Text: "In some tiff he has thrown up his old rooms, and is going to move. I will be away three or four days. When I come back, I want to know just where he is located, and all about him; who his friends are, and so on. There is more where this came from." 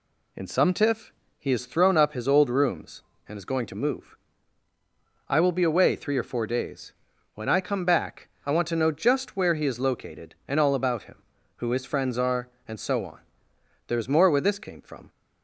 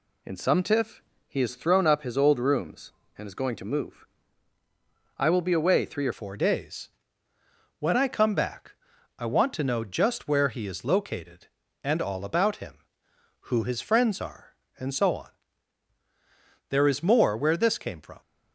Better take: first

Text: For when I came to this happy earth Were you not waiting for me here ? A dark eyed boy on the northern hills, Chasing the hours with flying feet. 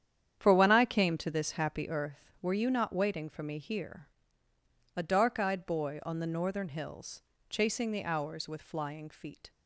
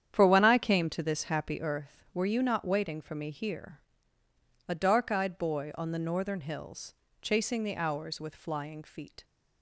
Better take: neither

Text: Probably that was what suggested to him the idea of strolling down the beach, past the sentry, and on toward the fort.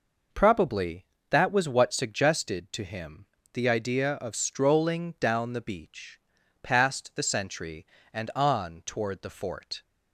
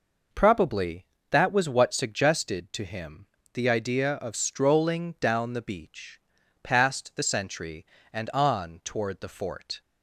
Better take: neither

